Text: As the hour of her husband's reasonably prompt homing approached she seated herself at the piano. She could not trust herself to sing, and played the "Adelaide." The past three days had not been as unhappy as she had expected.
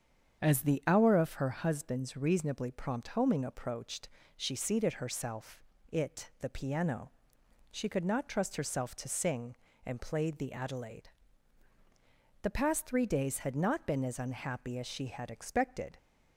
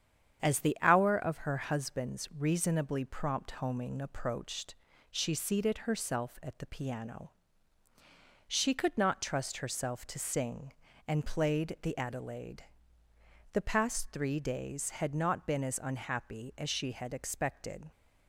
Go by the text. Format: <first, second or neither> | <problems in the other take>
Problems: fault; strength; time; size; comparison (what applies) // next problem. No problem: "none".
second | starts louder than the rest; strong; until 1.4 s; 7.5 dB; strong in the second // pauses between "approached" and "she"; slight; at 4.0 s; 0.30 s long; slight in the second // says "it" for "at"; at 5.9 s